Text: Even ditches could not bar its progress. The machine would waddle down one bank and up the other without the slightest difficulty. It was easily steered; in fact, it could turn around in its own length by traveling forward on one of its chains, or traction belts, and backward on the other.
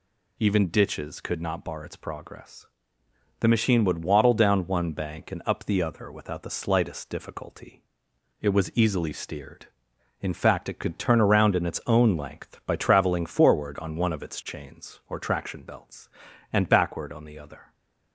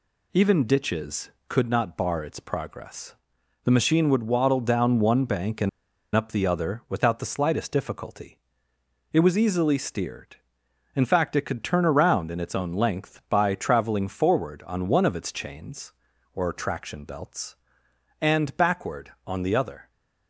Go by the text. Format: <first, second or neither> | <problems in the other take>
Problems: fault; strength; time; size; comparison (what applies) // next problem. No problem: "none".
first | pauses between "and" and "up"; noticeable; at 5.6 s; 0.46 s long